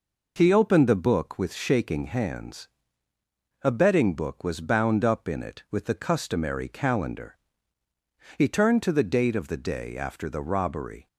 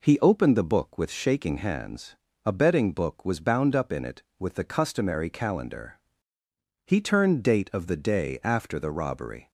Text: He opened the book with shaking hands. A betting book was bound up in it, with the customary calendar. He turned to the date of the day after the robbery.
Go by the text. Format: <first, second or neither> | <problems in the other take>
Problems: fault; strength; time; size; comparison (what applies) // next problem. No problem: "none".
first | skips "to the"; at 7.4 s